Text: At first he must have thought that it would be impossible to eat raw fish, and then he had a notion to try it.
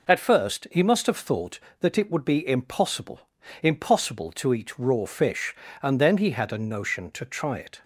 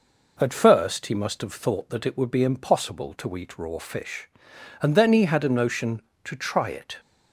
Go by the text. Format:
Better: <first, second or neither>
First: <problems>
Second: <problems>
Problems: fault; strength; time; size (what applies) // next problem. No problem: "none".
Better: second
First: says "impossible" twice; at 3.6 s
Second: none